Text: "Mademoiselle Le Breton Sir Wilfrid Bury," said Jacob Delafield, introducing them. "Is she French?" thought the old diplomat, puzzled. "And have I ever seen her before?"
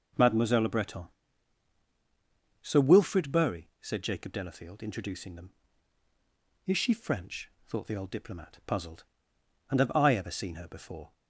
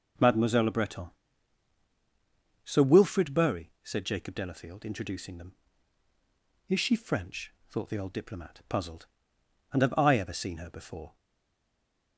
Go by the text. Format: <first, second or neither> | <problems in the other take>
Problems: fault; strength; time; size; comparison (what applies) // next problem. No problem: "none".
first | pauses between "Breton" and "Sir"; strong; at 1.0 s; 1.5 s long; strong in the first // stays silent after the last word; from 11.1 s on; 1.0 s long